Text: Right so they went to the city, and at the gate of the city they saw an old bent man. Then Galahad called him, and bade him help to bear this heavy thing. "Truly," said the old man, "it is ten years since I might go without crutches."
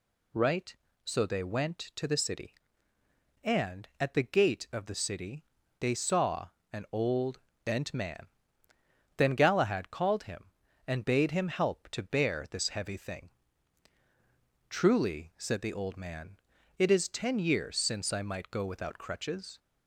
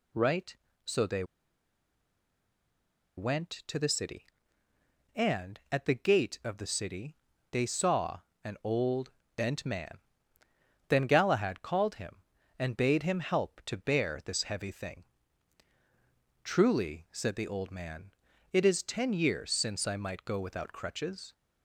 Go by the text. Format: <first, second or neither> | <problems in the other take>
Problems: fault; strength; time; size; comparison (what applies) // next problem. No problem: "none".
first | pauses between "they" and "went"; strong; at 1.2 s; 1.9 s long // pauses between "city" and "they"; slight; at 7.1 s; 0.36 s long; slight in the first // pauses between "saw" and "an"; slight; at 8.1 s; 0.24 s long; slight in the first // pauses between "old" and "bent"; slight; at 9.1 s; 0.26 s long; slight in the first